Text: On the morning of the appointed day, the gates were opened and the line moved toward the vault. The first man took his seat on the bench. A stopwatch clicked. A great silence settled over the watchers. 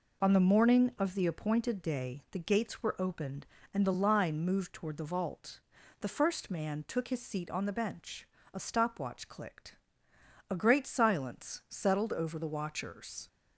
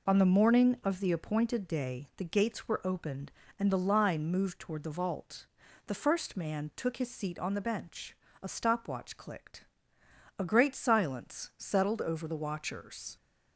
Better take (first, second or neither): neither